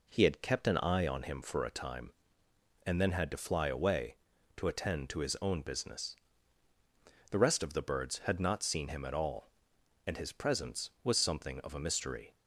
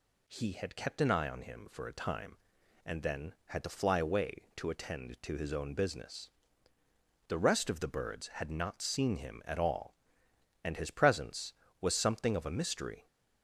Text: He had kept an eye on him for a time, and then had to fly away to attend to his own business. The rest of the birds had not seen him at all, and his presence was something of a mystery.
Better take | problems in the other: neither | none

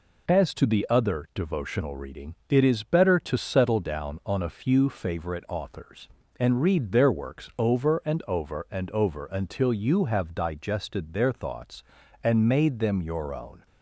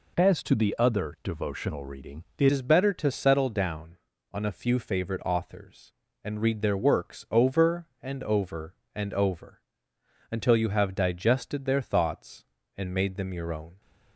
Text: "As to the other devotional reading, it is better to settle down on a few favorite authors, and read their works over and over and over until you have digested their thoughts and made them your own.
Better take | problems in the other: first | changes voice at "is"; from 2.5 s on; 11.3 s long // pauses between "over" and "until"; noticeable; at 9.6 s; 0.68 s long

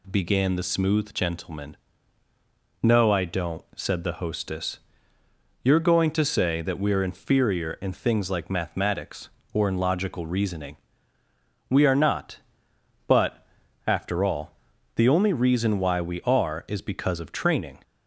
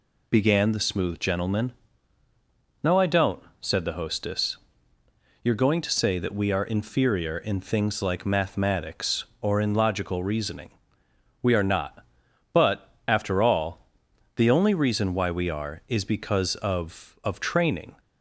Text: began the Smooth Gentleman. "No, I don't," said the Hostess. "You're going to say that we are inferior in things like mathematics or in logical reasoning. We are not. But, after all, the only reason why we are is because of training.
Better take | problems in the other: first | says "of" twice; at 17.2 s

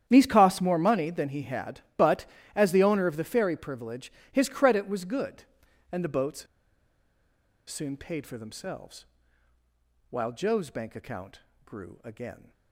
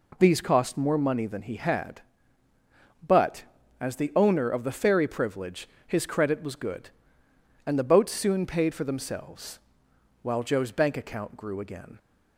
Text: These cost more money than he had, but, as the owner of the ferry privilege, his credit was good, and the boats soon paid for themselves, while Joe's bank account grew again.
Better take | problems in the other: second | starts louder than the rest; strong; until 1.0 s; 10 dB // pauses between "boats" and "soon"; at 6.4 s; 1.2 s long // pauses between "account" and "grew"; slight; at 11.3 s; 0.26 s long

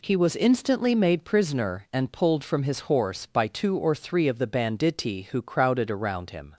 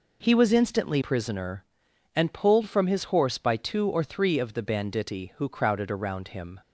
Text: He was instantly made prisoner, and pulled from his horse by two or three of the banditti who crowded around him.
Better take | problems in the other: first | skips "made"; at 1.0 s

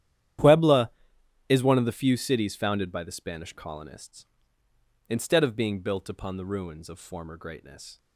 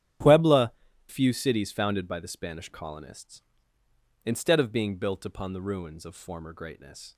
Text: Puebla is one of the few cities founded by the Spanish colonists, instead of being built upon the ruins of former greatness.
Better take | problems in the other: first | starts louder than the rest; strong; until 1.5 s; 10 dB; strong in the first // skips "is one of the"; at 0.9 s

